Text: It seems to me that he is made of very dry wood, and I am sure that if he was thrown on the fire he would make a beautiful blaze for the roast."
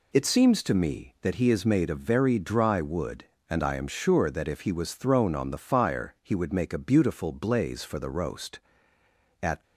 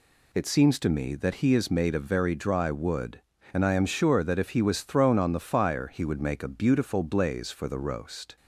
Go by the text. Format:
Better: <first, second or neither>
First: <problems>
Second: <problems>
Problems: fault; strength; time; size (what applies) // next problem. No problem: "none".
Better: second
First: goes on to say "At"; slight; from 9.4 s on; 0.20 s long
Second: none